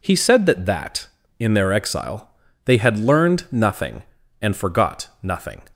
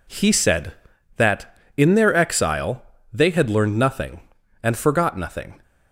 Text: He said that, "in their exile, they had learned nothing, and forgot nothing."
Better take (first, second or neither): second